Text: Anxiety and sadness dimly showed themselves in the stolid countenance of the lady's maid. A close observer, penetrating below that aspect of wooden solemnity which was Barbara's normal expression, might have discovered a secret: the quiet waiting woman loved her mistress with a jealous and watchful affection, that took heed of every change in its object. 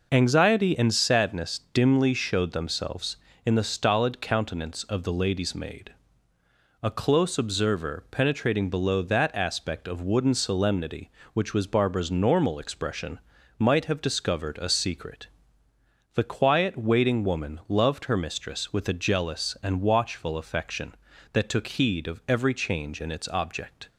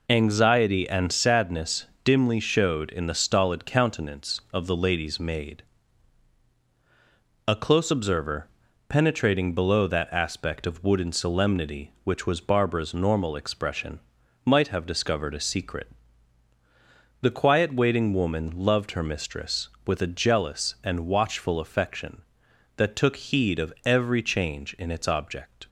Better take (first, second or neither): first